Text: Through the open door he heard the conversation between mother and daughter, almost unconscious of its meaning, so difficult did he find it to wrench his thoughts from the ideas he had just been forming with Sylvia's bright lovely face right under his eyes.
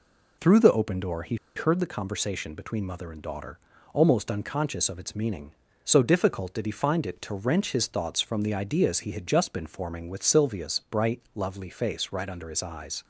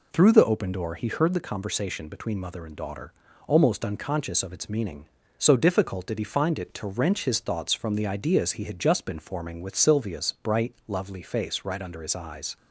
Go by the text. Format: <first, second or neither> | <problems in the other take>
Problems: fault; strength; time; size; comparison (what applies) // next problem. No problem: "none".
second | pauses between "he" and "heard"; slight; at 1.3 s; 0.20 s long